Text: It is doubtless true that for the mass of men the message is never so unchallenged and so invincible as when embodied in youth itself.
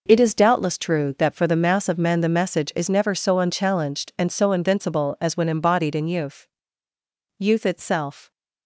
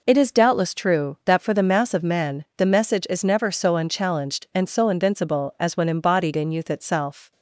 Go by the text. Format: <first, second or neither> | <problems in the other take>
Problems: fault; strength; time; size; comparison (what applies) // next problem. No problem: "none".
second | says "youth" twice; at 7.3 s